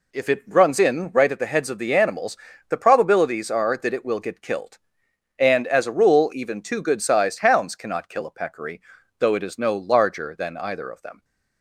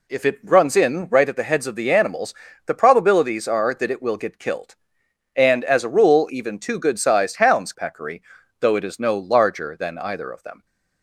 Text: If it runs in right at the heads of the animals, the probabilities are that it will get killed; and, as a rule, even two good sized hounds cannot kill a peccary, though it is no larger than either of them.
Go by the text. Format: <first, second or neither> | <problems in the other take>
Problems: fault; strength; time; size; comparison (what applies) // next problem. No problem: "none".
first | skips "cannot kill a"; at 7.7 s